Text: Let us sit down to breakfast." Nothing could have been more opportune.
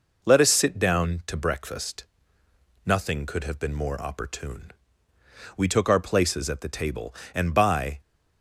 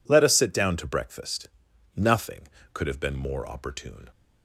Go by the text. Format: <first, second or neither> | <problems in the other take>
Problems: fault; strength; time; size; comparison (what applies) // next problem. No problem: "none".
second | goes on to say "We took our places at the table and by"; strong; from 5.5 s on; 2.4 s long